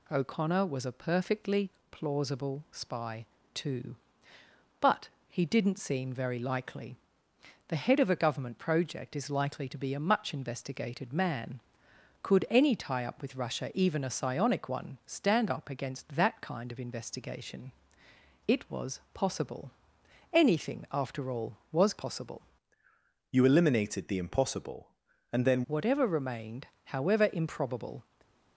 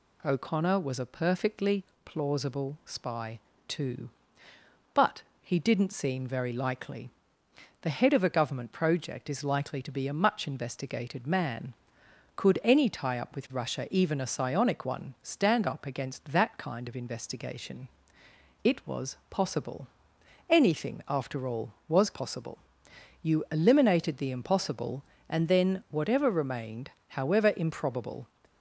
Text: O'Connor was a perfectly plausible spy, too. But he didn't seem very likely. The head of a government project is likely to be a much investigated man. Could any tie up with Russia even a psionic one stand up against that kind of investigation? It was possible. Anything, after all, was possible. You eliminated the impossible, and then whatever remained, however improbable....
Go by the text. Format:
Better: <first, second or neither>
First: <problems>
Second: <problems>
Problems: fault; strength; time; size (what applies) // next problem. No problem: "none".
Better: second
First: pauses between "perfectly" and "plausible"; slight; at 1.6 s; 0.22 s long // pauses between "But" and "he"; slight; at 5.0 s; 0.18 s long // changes voice from "You" to "then"; from 23.3 to 25.6 s; 2.3 s long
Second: pauses between "perfectly" and "plausible"; slight; at 1.8 s; 0.22 s long // pauses between "But" and "he"; slight; at 5.2 s; 0.18 s long